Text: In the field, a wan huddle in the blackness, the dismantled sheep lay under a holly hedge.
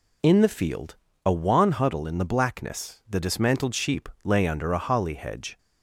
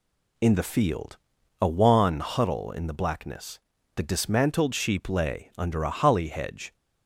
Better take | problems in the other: neither | none

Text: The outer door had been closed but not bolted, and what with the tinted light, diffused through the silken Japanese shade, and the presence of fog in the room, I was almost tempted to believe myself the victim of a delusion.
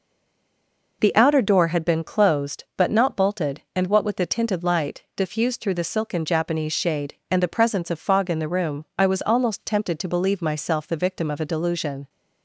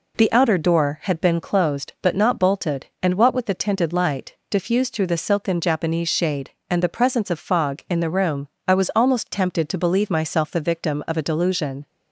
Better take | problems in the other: second | stays silent before the first word; until 1.0 s; 1.0 s long

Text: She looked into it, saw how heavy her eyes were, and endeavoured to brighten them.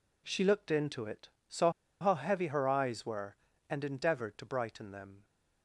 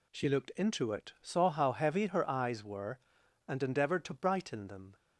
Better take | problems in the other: second | pauses between "saw" and "how"; slight; at 1.6 s; 0.31 s long

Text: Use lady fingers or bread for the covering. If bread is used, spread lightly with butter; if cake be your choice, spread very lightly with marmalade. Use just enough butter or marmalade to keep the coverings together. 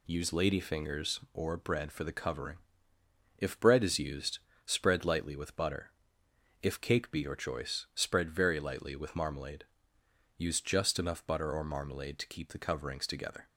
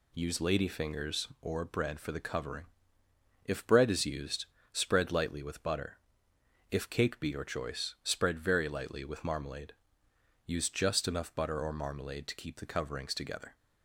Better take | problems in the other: neither | none

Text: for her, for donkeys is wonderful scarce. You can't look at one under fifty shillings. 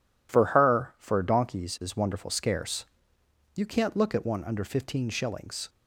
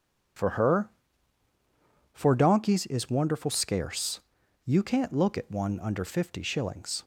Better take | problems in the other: second | says "fifteen" for "fifty"; at 4.6 s

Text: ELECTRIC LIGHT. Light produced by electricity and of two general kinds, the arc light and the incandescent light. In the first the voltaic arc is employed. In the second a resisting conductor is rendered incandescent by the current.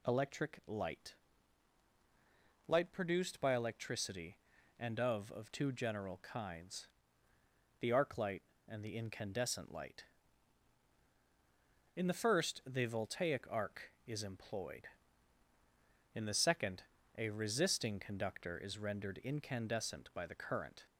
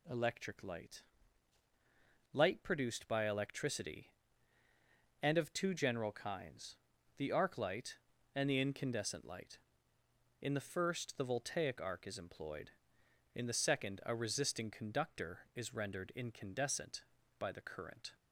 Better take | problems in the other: second | says "of" twice; at 5.3 s // pauses between "second" and "a"; slight; at 16.8 s; 0.34 s long

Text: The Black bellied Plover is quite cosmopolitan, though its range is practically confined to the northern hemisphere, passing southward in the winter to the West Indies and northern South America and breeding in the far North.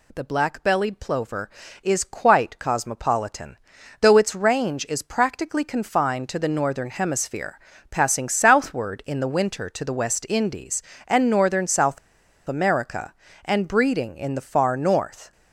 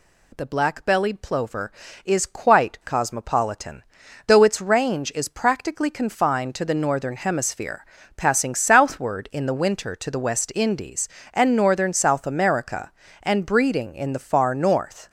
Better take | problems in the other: second | pauses between "South" and "America"; noticeable; at 11.9 s; 0.50 s long

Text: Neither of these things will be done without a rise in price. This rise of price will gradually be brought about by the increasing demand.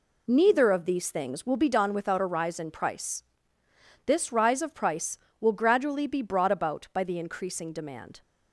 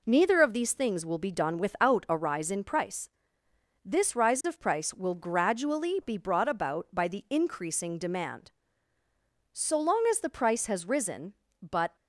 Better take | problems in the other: first | goes on to say "So long as the price has risen but"; strong; from 9.5 s on; 2.4 s long

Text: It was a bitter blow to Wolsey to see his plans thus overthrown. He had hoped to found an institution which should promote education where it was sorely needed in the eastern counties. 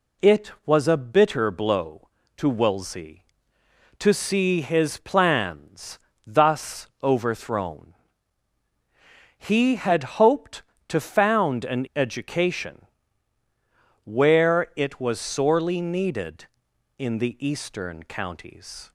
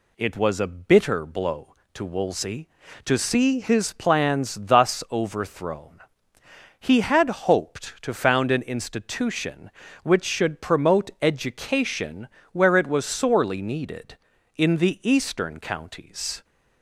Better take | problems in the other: second | pauses between "plans" and "thus"; slight; at 5.9 s; 0.26 s long // pauses between "thus" and "overthrown"; slight; at 6.8 s; 0.16 s long // skips "institution which should promote"; at 11.8 s // pauses between "education" and "where"; at 12.8 s; 1.2 s long; slight in the second

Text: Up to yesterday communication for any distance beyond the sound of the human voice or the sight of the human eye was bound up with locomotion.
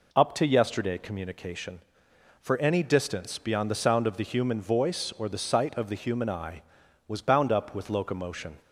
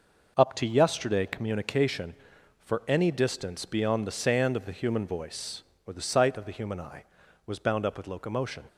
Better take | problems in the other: first | says "sand" for "sound"; at 4.1 s

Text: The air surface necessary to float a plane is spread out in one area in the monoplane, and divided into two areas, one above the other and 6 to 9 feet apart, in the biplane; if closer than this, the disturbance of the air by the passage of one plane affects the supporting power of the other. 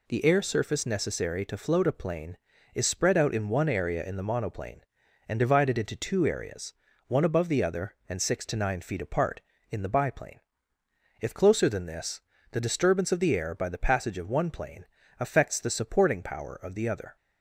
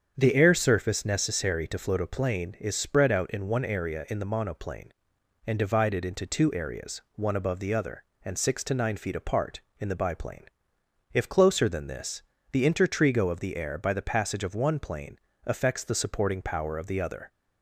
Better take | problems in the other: first | starts louder than the rest; strong; until 1.1 s; 7.5 dB // says "intertrigo" for "disturbance"; at 12.6 s // pauses between "plane" and "affects"; slight; at 15.1 s; 0.28 s long; slight in the first

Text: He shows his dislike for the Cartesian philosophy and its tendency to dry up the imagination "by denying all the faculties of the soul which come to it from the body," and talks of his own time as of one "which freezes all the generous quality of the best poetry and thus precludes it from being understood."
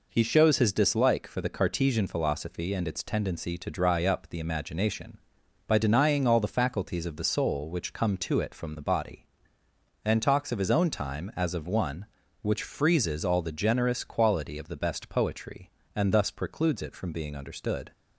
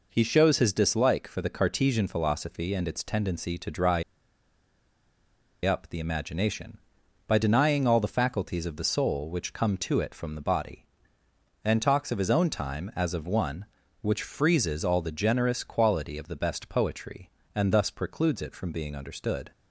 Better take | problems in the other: first | pauses between "dry" and "up"; strong; at 4.0 s; 1.6 s long

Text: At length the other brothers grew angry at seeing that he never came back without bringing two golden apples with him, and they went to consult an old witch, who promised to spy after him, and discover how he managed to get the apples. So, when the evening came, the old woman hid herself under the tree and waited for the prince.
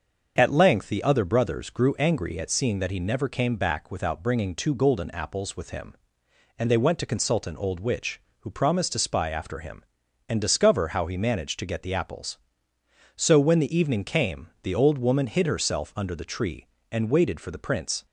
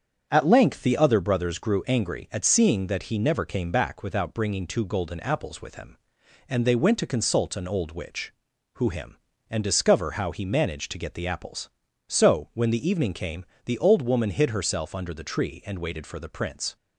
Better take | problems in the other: first | starts louder than the rest; strong; until 1.3 s; 7.5 dB; also in the first // skips "promised to spy after"; at 8.8 s

